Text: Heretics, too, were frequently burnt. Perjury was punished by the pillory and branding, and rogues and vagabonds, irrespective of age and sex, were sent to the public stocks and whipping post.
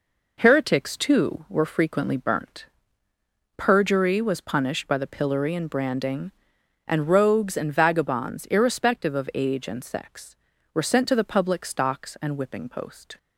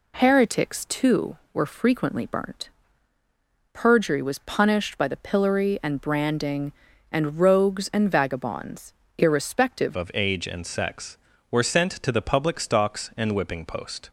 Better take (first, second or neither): first